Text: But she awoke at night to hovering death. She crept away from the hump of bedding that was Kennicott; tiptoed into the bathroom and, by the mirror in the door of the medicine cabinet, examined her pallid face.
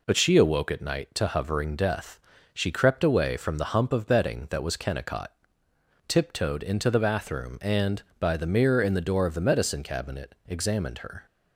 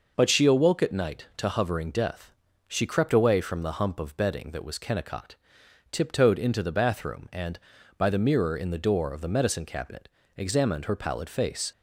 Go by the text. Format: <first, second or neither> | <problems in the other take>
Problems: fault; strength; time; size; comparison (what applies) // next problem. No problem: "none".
second | stops before "pallid face"; at 11.2 s